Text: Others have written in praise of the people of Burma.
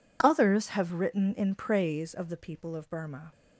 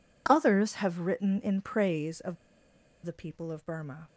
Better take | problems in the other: first | pauses between "of" and "the"; noticeable; at 2.3 s; 0.68 s long

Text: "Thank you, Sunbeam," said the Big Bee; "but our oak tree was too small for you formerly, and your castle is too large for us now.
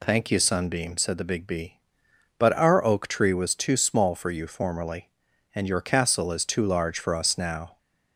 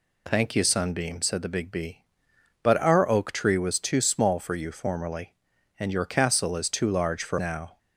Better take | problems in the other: first | skips "us"; at 7.3 s

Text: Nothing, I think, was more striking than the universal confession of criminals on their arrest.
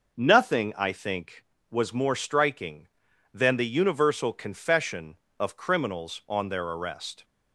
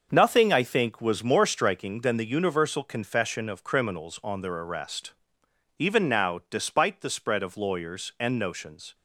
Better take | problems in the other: first | starts louder than the rest; until 1.1 s; 6.5 dB // goes on to say "Even now despite the spread of lawyers and notions"; strong; from 5.7 s on; 3.1 s long

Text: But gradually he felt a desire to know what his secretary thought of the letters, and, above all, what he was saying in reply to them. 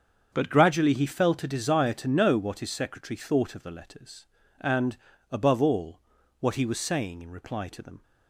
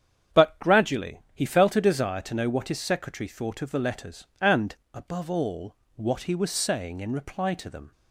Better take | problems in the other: neither | starts louder than the rest; strong; the same in both

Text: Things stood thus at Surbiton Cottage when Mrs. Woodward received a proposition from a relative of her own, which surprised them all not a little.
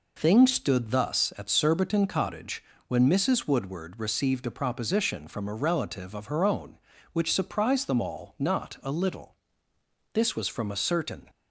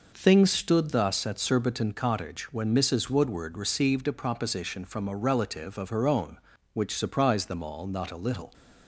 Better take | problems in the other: second | pauses between "Cottage" and "when"; slight; at 2.6 s; 0.24 s long // goes on to say "This was from a certain"; noticeable; from 10.1 s on; 1.1 s long

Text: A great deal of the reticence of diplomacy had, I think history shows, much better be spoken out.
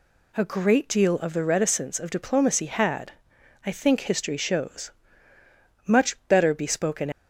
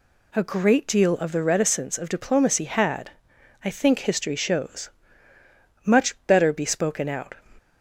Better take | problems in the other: second | stops before "out"; at 7.1 s

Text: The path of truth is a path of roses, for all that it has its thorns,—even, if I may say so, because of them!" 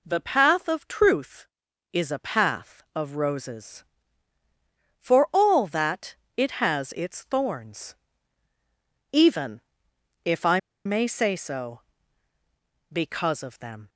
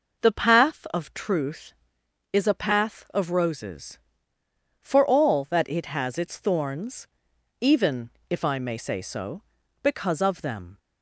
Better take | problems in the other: second | pauses between "that" and "it"; slight; at 6.1 s; 0.18 s long // pauses between "I" and "may"; slight; at 10.5 s; 0.26 s long

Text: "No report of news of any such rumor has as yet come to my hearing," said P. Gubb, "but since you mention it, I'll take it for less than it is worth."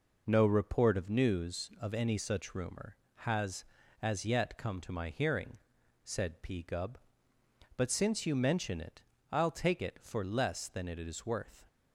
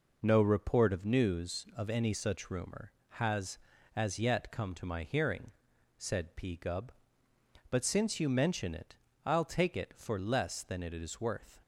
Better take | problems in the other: neither | none

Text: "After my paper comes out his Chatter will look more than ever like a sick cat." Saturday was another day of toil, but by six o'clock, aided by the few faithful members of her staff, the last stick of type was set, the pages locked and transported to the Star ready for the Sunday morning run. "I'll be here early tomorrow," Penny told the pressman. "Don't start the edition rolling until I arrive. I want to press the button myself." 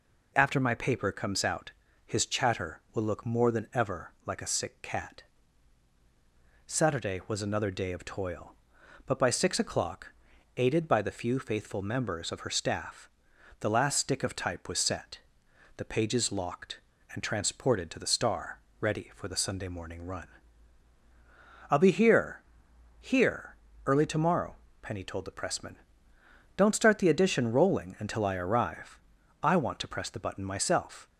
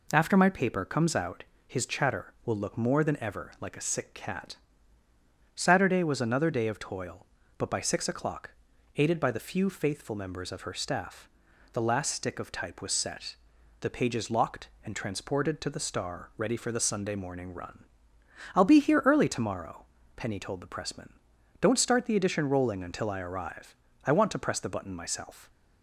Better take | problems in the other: second | pauses between "out" and "his"; slight; at 1.7 s; 0.34 s long; slight in the second // pauses between "Star" and "ready"; slight; at 18.5 s; 0.22 s long // says "here" twice; at 23.0 s

